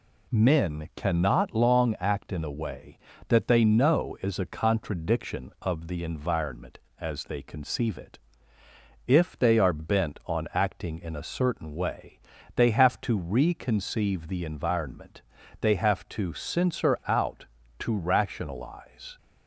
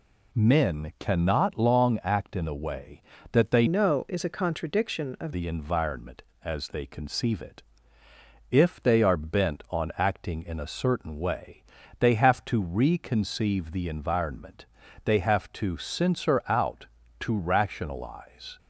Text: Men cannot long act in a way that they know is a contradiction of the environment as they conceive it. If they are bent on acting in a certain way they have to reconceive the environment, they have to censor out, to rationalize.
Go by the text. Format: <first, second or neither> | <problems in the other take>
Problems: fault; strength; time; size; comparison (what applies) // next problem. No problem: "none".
first | changes voice from "know" to "of"; from 3.6 to 5.3 s; 1.7 s long // pauses between "way" and "they"; at 11.6 s; 0.38 s long; also in the first